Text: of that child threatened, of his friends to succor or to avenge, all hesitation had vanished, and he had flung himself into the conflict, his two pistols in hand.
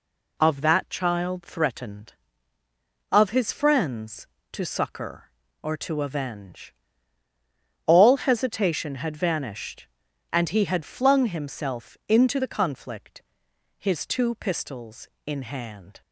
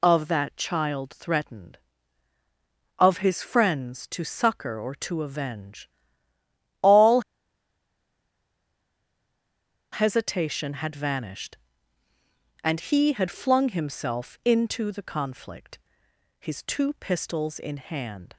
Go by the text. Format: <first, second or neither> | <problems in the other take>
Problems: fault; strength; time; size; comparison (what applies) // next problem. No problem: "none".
first | pauses between "all" and "hesitation"; strong; at 7.2 s; 2.7 s long